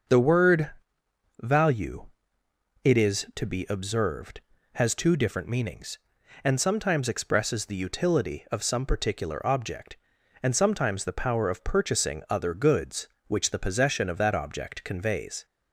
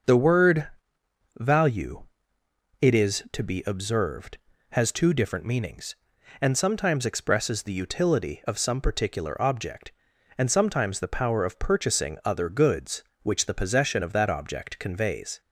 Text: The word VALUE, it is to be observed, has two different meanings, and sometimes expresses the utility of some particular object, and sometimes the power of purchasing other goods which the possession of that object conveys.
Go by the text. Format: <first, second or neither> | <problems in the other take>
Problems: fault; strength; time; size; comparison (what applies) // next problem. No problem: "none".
neither | starts louder than the rest; the same in both // pauses between "word" and "VALUE"; noticeable; the same in both